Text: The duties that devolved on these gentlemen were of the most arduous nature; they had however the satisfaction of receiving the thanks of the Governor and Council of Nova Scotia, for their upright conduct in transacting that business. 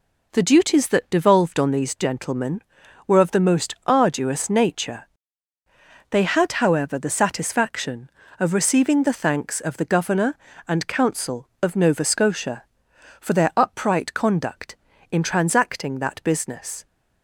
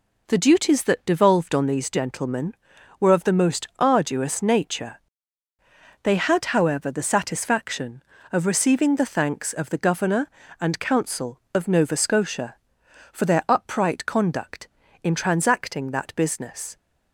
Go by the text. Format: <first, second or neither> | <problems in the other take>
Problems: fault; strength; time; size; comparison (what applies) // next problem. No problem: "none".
neither | none